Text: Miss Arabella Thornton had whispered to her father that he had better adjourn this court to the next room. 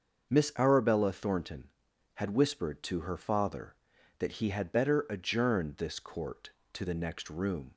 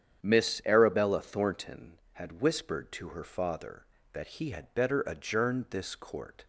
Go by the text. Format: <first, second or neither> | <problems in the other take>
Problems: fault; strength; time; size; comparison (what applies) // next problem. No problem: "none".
first | starts louder than the rest; strong; until 1.2 s; 9 dB; also in the first // stops before "to the next room"; at 6.4 s